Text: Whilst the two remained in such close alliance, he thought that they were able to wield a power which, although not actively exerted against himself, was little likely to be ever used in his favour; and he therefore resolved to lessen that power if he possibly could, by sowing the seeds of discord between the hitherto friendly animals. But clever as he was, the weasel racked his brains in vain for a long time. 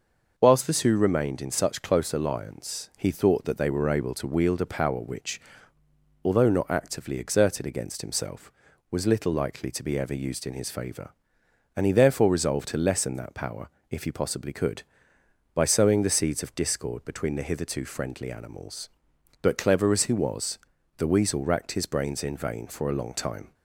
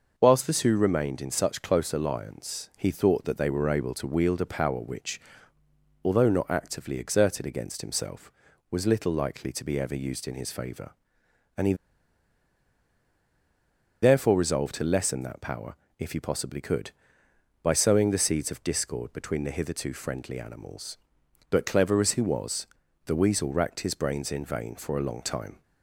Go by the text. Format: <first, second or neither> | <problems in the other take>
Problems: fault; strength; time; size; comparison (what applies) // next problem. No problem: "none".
first | pauses between "he" and "therefore"; strong; at 11.7 s; 2.2 s long // pauses between "power" and "if"; slight; at 15.7 s; 0.24 s long; slight in the first